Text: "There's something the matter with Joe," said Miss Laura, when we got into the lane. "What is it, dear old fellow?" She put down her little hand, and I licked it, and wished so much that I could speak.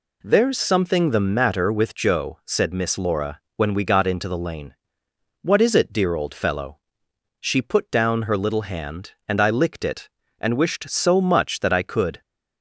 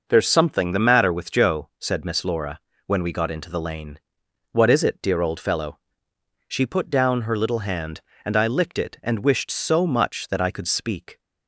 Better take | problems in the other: second | stops before "speak"; at 12.2 s

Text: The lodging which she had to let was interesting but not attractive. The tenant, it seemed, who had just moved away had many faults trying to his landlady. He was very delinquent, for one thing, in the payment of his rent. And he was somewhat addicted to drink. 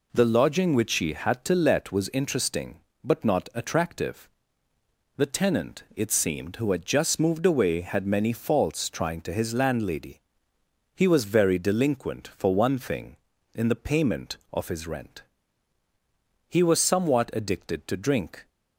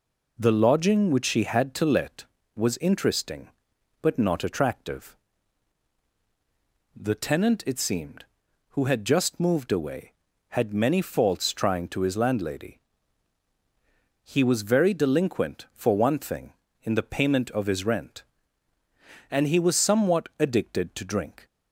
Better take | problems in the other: second | skips "And"; at 15.8 s

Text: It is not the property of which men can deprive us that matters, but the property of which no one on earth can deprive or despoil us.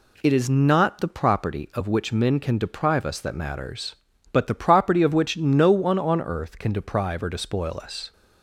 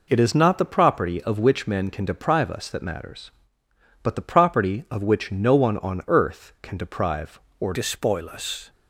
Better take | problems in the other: first | changes voice at "despoil"; from 7.7 s on; 0.9 s long

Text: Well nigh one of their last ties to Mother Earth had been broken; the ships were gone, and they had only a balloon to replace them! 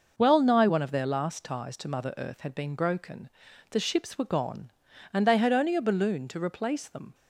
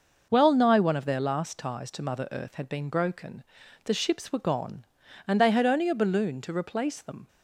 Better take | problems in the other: neither | none

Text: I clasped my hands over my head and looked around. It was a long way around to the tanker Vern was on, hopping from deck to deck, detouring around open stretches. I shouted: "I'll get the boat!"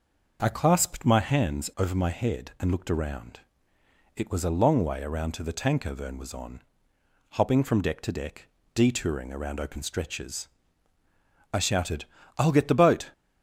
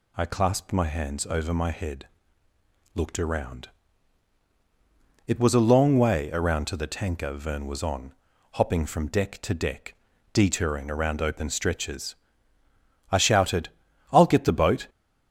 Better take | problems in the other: first | skips "and"; at 2.5 s

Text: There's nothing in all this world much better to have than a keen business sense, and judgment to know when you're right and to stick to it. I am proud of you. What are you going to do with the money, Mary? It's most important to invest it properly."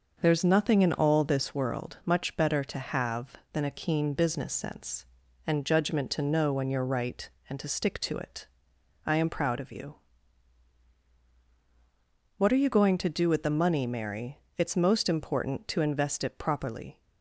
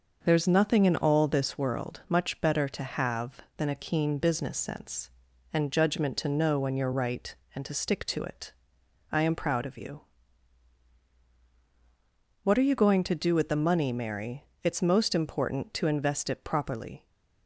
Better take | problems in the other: neither | none

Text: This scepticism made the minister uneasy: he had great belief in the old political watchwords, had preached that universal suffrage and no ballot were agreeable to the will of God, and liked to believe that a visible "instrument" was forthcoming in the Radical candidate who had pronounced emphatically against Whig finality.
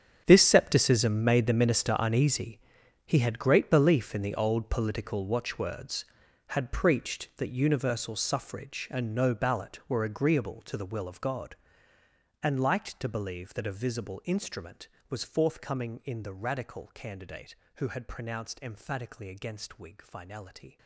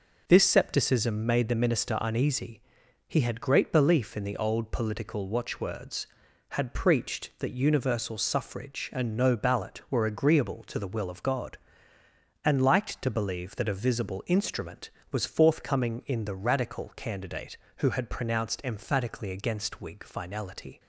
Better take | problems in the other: second | gets quieter; strong; throughout; 16 dB

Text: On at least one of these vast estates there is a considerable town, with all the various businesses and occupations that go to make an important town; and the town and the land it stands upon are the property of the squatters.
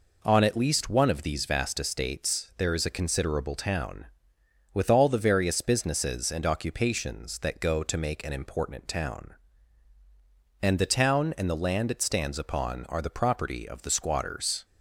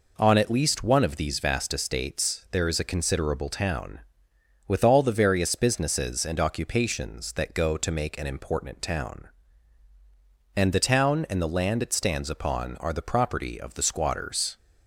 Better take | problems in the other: neither | none

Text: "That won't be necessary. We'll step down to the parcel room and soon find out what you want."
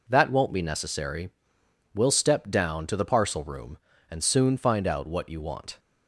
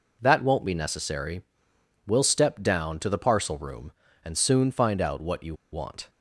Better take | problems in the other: first | pauses between "you" and "want"; slight; at 5.5 s; 0.17 s long

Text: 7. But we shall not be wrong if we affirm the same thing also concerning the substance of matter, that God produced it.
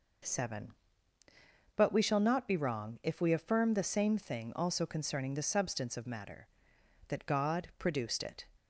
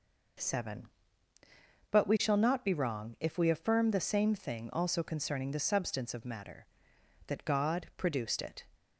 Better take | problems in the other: neither | none

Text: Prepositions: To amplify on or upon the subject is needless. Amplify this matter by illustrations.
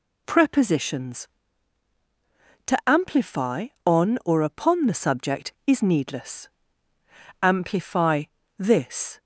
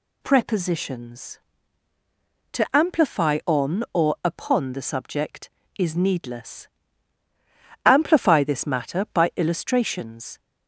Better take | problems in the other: second | pauses between "Amplify" and "this"; slight; at 8.2 s; 0.34 s long // stops before "matter by illustrations"; at 9.1 s

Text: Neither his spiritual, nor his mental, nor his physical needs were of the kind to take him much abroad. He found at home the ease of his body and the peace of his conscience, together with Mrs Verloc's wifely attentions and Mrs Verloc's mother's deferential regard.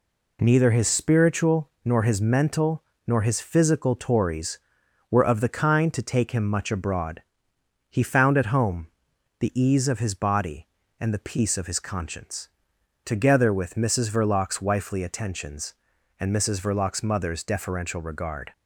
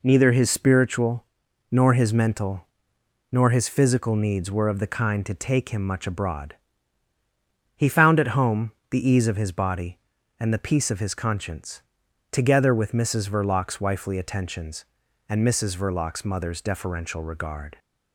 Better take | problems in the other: second | says "tories" for "needs"; at 3.9 s // pauses between "home" and "the"; noticeable; at 8.8 s; 0.54 s long; slight in the second

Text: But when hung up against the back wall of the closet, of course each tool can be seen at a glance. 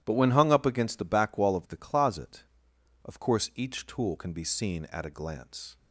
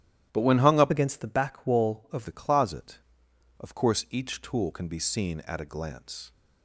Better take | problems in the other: first | starts louder than the rest; strong; until 1.3 s; 12 dB; strong in the first // changes voice from "against" to "of"; from 0.9 to 2.2 s; 1.3 s long

